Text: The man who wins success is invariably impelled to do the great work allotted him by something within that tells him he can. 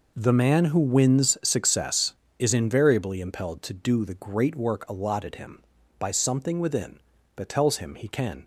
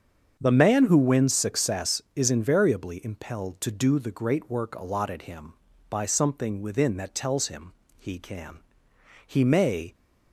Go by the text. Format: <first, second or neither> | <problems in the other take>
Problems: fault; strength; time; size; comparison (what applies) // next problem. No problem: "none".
first | starts louder than the rest; strong; until 1.4 s; 7 dB // pauses between "him" and "he"; slight; at 7.7 s; 0.26 s long // goes on to say "He may"; noticeable; from 9.2 s on; 0.66 s long